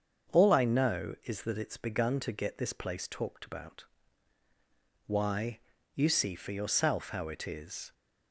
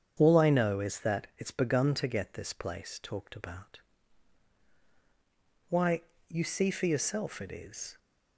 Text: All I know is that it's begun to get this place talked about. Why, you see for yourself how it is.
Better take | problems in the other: first | starts louder than the rest; strong; until 1.1 s; 8 dB; also in the first // skips "how"; at 7.3 s

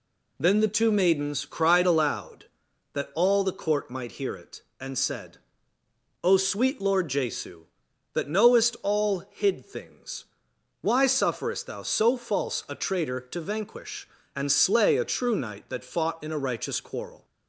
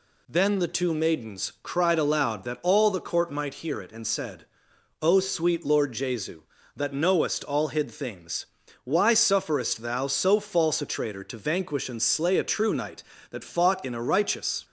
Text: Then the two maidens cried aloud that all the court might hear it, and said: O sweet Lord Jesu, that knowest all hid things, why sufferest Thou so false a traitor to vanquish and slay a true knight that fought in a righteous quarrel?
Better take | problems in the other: first | stops before "quarrel"; at 14.6 s

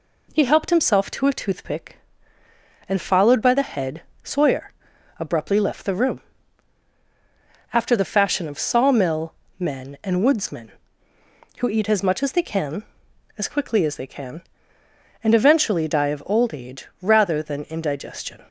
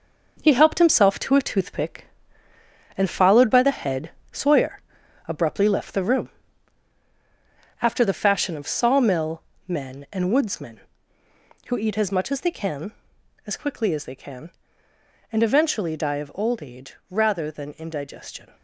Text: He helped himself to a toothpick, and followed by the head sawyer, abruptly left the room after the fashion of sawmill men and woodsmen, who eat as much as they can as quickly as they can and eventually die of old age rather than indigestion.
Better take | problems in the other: first | gets quieter; strong; throughout; 7.5 dB // pauses between "head" and "sawyer"; slight; at 4.0 s; 0.22 s long; slight in the first // pauses between "room" and "after"; strong; at 6.2 s; 1.5 s long; strong in the first // pauses between "sawmill" and "men"; slight; at 9.4 s; 0.26 s long; slight in the first

